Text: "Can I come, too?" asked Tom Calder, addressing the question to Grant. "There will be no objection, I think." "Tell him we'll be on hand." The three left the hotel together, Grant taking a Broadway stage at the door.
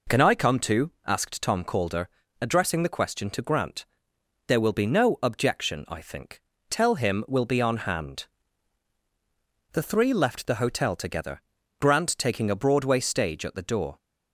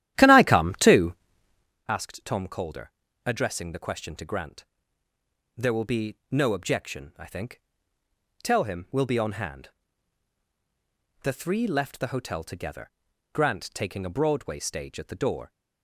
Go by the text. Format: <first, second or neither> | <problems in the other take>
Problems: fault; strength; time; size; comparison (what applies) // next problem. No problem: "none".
first | starts louder than the rest; strong; until 1.8 s; 13 dB